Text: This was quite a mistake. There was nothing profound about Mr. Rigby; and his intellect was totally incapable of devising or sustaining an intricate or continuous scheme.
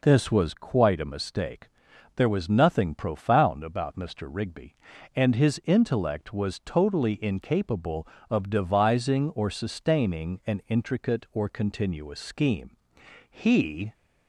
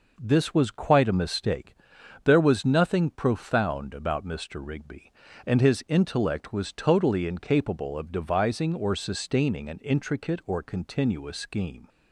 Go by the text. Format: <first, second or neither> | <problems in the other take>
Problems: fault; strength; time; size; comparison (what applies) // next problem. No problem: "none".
second | goes on to say "He"; noticeable; from 13.3 s on; 0.62 s long